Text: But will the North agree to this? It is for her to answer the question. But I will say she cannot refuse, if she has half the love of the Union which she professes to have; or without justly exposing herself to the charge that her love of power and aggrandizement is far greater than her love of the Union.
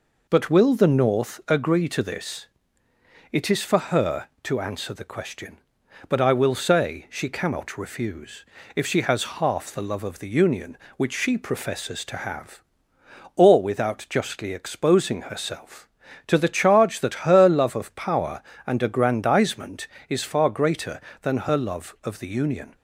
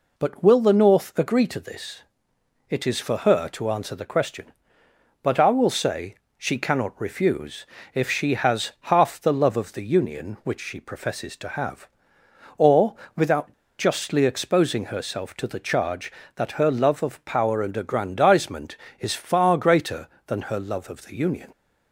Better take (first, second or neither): first